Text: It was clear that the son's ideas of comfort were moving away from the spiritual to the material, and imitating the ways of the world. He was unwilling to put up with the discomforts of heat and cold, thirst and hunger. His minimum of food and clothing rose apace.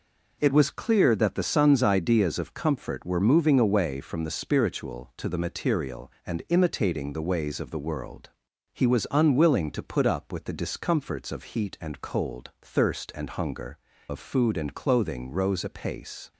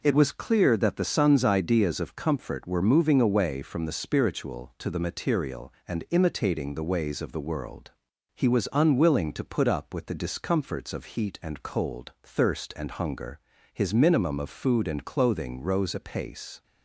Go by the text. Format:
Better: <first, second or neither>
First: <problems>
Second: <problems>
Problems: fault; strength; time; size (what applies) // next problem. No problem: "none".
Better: second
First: skips "His minimum"; at 13.9 s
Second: none